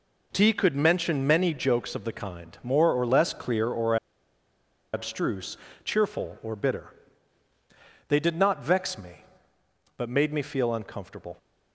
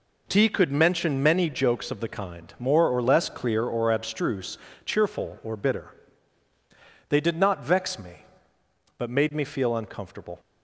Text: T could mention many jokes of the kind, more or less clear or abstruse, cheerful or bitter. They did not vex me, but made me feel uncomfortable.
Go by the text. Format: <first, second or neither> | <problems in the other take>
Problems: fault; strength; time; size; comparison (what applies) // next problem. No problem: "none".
second | pauses between "or" and "abstruse"; noticeable; at 3.9 s; 0.97 s long